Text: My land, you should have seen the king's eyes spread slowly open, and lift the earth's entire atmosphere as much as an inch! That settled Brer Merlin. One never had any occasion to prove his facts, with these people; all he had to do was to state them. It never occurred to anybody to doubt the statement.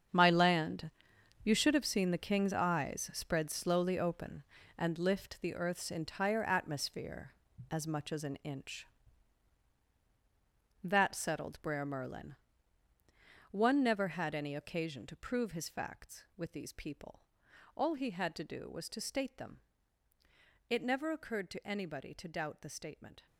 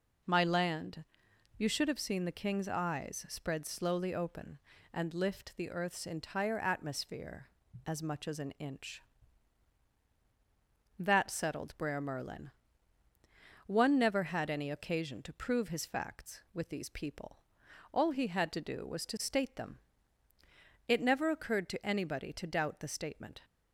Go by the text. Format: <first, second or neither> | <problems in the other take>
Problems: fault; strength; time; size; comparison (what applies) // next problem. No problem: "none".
second | gets quieter; strong; throughout; 13 dB